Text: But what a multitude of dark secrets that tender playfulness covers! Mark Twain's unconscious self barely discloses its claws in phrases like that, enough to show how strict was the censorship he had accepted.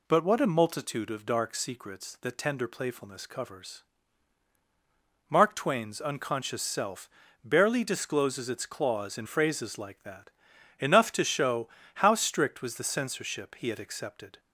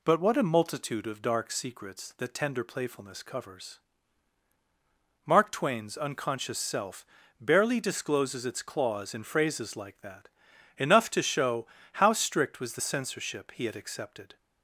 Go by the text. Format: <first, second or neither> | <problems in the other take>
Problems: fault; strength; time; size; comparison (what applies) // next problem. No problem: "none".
neither | pauses between "self" and "barely"; slight; the same in both // pauses between "show" and "how"; slight; the same in both